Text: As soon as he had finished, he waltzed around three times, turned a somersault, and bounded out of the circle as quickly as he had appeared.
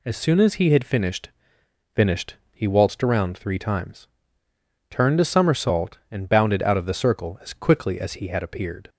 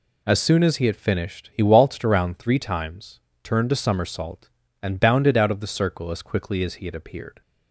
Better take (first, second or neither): second